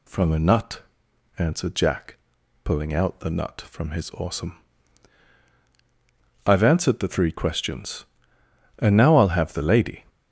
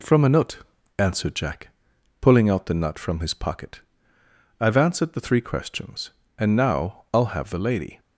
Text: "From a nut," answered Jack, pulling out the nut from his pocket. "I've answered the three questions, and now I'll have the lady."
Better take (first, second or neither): second